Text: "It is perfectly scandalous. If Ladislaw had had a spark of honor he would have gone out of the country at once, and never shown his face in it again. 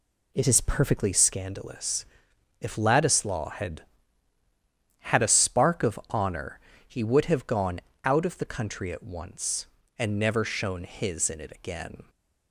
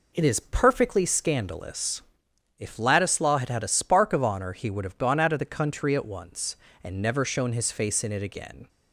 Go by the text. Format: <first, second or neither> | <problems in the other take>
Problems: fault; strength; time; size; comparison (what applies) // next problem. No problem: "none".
second | pauses between "honor" and "he"; slight; at 6.5 s; 0.30 s long // pauses between "gone" and "out"; slight; at 7.8 s; 0.24 s long // skips "face"; at 11.2 s